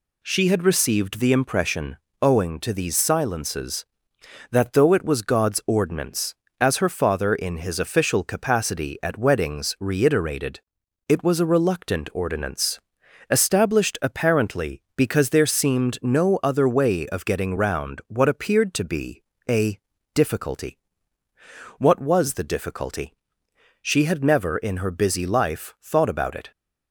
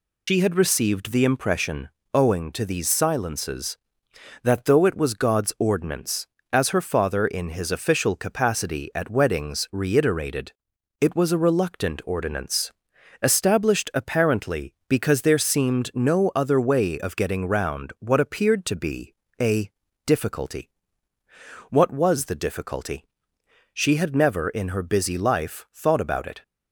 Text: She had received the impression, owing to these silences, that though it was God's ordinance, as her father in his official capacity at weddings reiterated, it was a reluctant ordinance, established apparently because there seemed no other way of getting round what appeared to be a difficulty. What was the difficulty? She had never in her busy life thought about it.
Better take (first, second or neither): first